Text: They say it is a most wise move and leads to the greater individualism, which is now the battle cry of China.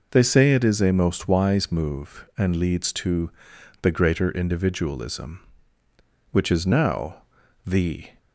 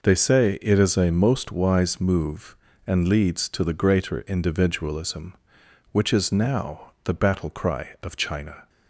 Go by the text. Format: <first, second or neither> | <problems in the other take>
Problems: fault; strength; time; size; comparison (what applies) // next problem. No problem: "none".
second | pauses between "to" and "the"; noticeable; at 3.2 s; 0.52 s long // pauses between "now" and "the"; at 7.2 s; 0.42 s long // stops before "battle cry of China"; at 8.1 s